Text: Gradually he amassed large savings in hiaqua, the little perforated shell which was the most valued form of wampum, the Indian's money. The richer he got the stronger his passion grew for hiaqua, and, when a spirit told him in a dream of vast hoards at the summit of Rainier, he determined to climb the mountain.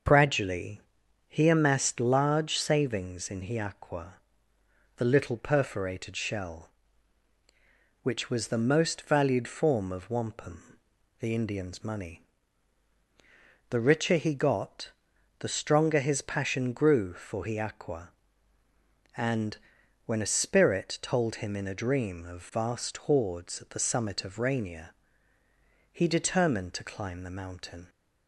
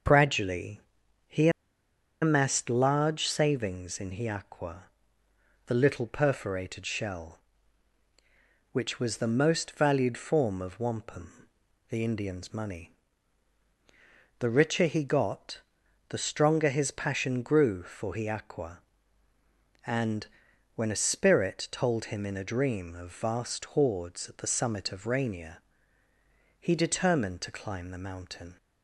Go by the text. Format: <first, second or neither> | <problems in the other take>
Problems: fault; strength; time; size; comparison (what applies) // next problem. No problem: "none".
first | starts louder than the rest; noticeable; until 2.2 s; 6 dB; also in the first // pauses between "Gradually" and "he"; noticeable; at 0.7 s; 0.48 s long; noticeable in the first // pauses between "he" and "amassed"; noticeable; at 1.4 s; 0.72 s long // pauses between "got" and "the"; noticeable; at 15.6 s; 0.48 s long; noticeable in the first